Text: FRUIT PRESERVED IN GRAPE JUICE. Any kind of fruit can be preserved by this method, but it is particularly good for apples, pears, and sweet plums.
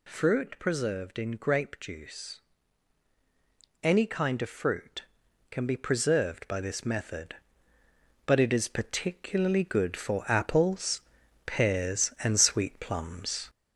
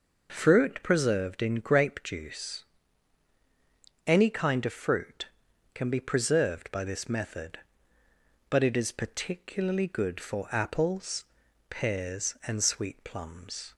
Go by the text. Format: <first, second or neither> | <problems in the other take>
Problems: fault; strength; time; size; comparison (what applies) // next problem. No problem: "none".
second | gets louder; noticeable; throughout; 4 dB